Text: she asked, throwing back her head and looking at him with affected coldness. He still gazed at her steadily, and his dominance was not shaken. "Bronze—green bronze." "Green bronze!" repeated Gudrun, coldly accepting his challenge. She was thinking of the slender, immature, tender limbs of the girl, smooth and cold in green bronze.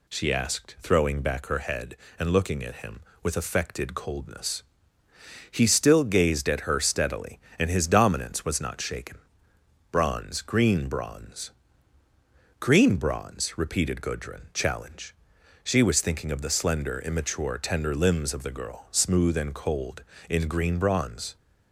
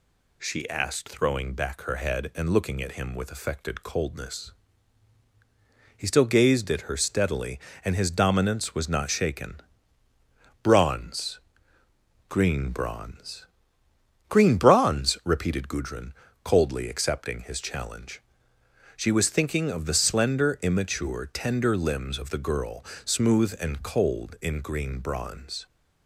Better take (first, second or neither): second